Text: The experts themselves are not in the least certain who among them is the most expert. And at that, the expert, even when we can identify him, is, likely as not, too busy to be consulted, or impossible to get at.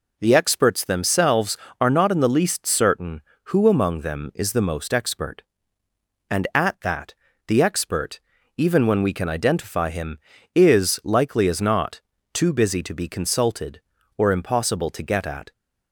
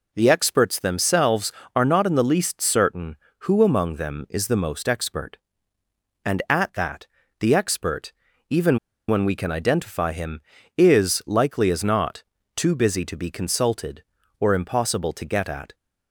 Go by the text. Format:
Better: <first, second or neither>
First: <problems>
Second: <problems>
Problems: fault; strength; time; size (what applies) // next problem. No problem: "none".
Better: first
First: none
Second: pauses between "even" and "when"; slight; at 8.7 s; 0.29 s long